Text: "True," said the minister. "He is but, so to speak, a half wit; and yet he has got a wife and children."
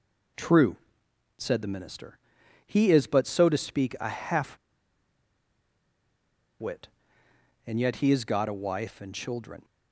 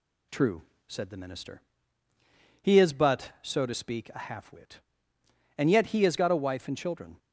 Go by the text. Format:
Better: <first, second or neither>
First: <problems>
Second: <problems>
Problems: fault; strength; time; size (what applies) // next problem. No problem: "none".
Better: second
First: pauses between "half" and "wit"; strong; at 4.5 s; 2.0 s long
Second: none